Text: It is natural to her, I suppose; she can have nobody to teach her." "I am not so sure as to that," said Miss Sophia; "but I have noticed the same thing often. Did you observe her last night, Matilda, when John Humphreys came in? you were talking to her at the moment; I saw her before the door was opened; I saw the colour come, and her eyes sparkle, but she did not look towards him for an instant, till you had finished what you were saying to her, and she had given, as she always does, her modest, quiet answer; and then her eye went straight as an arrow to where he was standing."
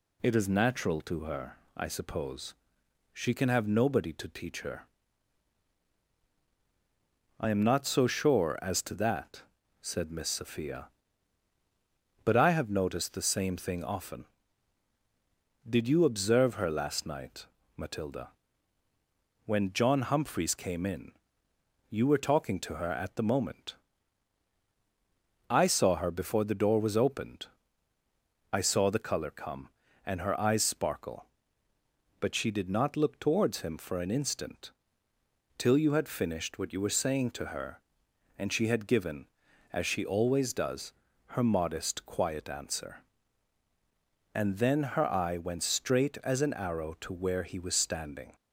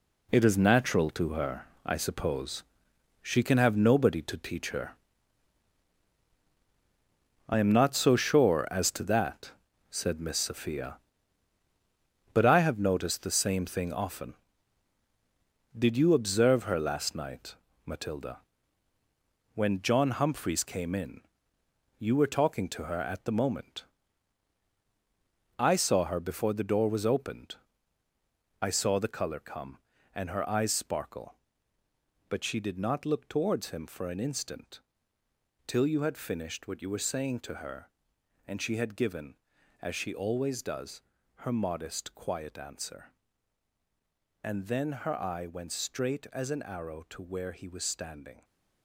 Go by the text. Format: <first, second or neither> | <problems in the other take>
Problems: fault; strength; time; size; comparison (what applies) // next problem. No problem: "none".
first | gets quieter; strong; throughout; 9 dB